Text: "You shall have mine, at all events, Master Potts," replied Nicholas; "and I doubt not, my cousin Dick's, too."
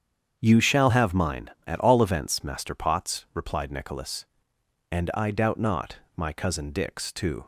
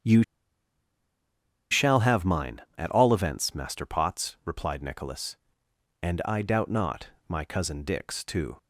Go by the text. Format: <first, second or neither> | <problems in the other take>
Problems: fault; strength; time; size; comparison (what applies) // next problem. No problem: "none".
first | starts louder than the rest; strong; until 2.5 s; 8 dB; strong in the first // pauses between "You" and "shall"; strong; at 0.2 s; 1.4 s long